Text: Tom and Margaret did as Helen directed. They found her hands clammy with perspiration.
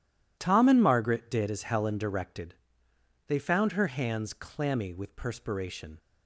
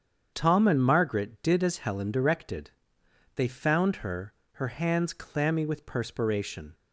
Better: first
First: none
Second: starts louder than the rest; strong; until 1.3 s; 8 dB // says "her" twice; at 4.5 s

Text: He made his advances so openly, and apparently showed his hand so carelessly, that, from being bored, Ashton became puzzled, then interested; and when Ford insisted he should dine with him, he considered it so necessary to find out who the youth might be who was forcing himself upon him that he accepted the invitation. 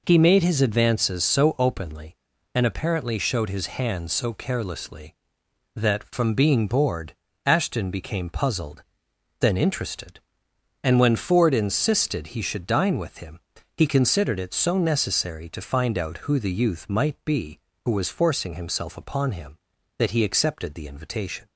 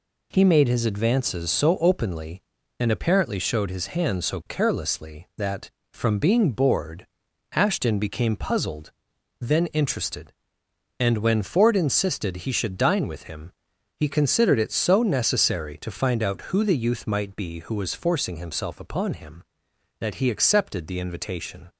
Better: neither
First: none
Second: none

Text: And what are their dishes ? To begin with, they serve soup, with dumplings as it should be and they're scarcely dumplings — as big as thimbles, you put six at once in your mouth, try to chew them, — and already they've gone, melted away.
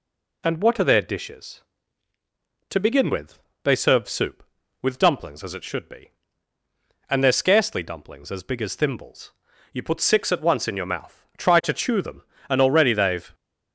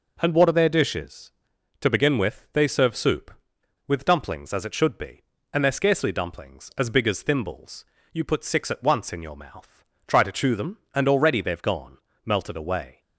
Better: second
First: stops before "gone melted away"; at 13.3 s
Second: none

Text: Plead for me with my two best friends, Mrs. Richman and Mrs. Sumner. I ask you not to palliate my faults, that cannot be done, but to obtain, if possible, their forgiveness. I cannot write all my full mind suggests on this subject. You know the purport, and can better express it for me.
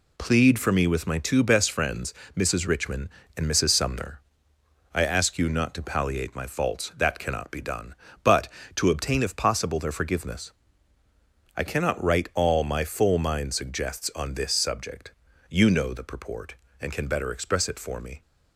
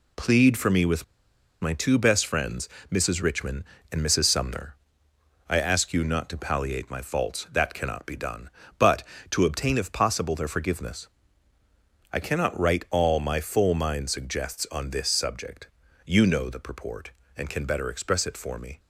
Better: first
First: none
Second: pauses between "with" and "my"; noticeable; at 1.0 s; 0.56 s long

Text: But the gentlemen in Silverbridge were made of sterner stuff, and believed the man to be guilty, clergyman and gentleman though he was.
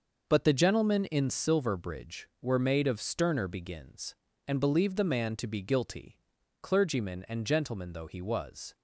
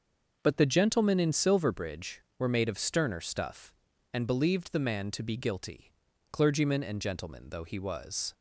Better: second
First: starts louder than the rest; noticeable; until 1.2 s; 6 dB // says "begins" for "stuff"; at 3.4 s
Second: starts louder than the rest; noticeable; until 1.4 s; 6 dB

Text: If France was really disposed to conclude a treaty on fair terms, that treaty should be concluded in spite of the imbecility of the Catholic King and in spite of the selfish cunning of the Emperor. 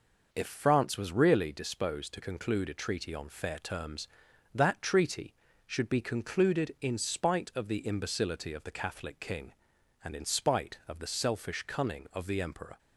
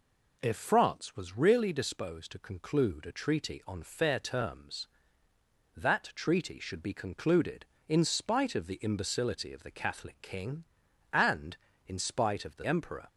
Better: first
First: none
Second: skips "selfish cunning of the"; at 12.6 s

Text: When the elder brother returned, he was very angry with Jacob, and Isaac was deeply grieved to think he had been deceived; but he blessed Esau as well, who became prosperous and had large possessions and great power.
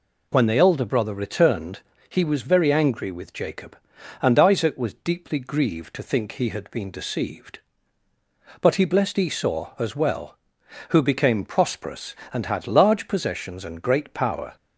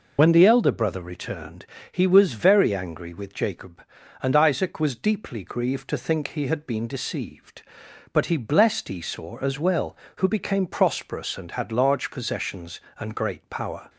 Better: first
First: none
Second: loses the start of "When"; at 0.1 s; 65 ms

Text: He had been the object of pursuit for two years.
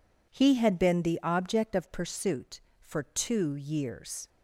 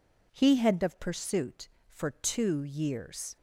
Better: first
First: none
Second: skips "been the object"; at 0.8 s

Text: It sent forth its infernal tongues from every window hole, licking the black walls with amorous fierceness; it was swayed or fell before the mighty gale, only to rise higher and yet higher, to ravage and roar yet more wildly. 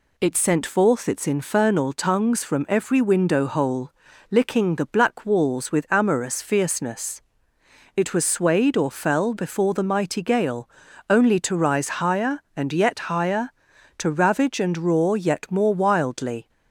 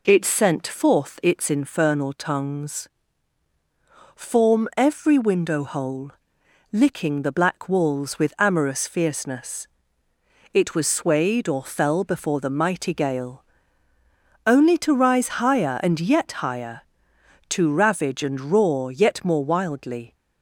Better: first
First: none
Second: says "form" for "from"; at 4.1 s

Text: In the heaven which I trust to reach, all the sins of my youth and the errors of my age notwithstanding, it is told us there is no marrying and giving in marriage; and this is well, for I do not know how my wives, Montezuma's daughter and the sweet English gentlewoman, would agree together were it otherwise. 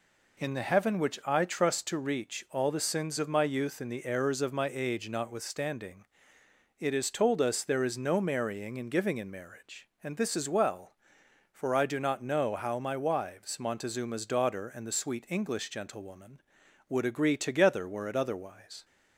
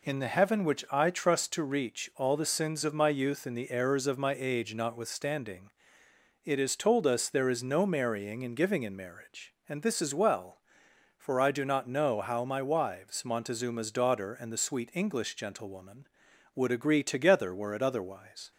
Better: neither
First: none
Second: none

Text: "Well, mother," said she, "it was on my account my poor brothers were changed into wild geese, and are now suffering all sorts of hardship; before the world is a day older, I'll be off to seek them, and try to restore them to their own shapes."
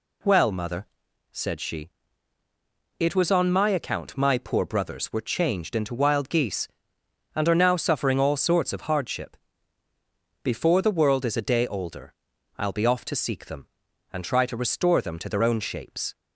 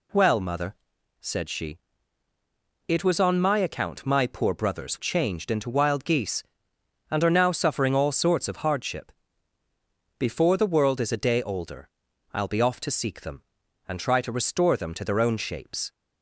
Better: first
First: none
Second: skips "were"; at 4.9 s

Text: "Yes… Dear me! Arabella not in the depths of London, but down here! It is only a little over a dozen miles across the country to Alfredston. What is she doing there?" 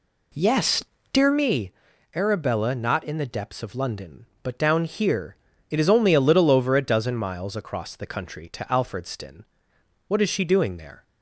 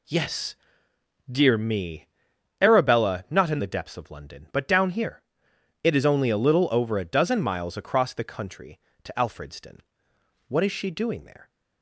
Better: second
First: starts louder than the rest; slight; until 1.5 s; 2 dB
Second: none

